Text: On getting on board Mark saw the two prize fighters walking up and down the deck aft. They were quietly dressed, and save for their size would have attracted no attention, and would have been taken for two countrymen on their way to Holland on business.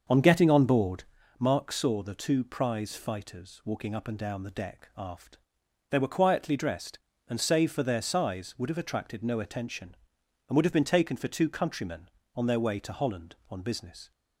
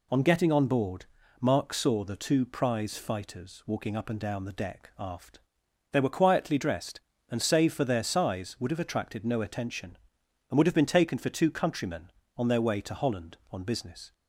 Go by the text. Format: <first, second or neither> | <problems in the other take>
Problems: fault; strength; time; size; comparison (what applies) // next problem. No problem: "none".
second | starts louder than the rest; until 1.3 s; 6.5 dB // pauses between "board" and "Mark"; slight; at 1.0 s; 0.34 s long; slight in the second